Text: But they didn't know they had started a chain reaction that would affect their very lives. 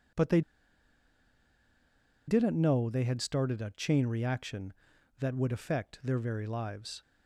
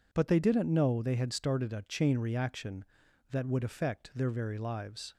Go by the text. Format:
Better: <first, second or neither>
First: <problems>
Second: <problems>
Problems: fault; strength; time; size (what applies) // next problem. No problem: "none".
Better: second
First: pauses between "they" and "didn't"; strong; at 0.4 s; 1.8 s long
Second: none